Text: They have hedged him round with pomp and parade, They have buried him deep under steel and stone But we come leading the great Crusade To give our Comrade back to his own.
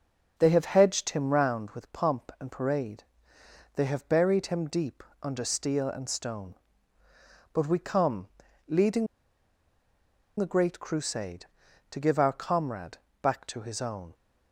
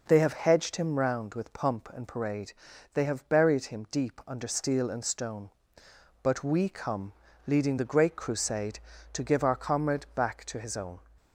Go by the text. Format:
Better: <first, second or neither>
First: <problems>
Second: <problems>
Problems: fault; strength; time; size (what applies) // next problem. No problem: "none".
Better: second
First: starts louder than the rest; noticeable; until 1.4 s; 6 dB // pauses between "deep" and "under"; slight; at 5.0 s; 0.20 s long // pauses between "come" and "leading"; at 8.2 s; 0.40 s long // pauses between "leading" and "the"; strong; at 9.0 s; 1.3 s long // pauses between "Comrade" and "back"; slight; at 12.9 s; 0.22 s long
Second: pauses between "come" and "leading"; slight; at 7.1 s; 0.34 s long